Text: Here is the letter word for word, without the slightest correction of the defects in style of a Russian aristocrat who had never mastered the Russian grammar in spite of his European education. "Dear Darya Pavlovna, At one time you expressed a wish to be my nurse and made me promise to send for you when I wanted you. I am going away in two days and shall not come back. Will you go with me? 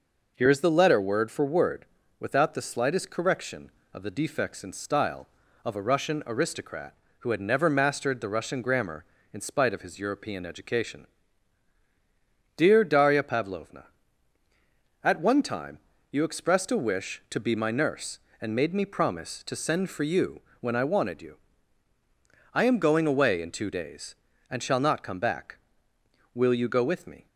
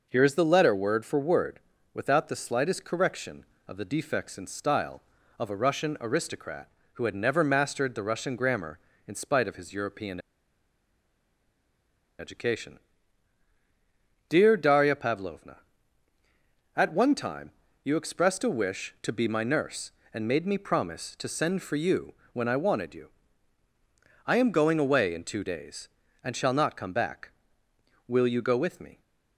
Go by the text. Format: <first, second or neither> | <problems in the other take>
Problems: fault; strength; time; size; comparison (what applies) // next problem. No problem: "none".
first | pauses between "European" and "education"; strong; at 10.1 s; 2.0 s long // pauses between "time" and "you"; slight; at 17.5 s; 0.32 s long; slight in the first // pauses between "you" and "when"; slight; at 22.1 s; 0.18 s long; slight in the first